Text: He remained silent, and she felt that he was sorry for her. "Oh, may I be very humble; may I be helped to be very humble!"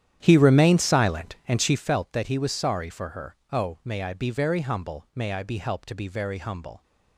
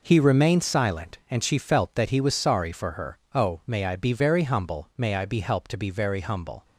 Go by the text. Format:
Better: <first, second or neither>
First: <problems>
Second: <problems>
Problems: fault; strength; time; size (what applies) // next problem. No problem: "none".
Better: second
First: starts louder than the rest; strong; until 1.9 s; 10.5 dB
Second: none